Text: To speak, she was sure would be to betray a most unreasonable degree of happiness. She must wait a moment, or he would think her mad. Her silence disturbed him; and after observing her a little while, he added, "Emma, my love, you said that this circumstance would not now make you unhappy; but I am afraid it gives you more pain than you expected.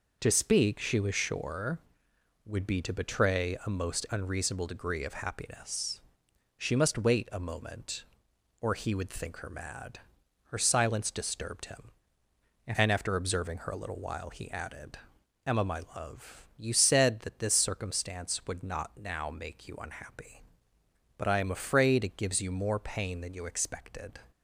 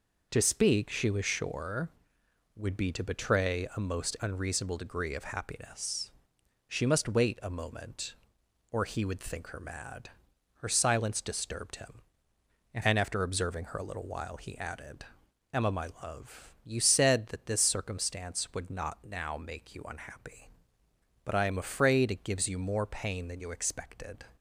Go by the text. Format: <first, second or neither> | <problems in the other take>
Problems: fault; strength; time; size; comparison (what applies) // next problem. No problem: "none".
neither | none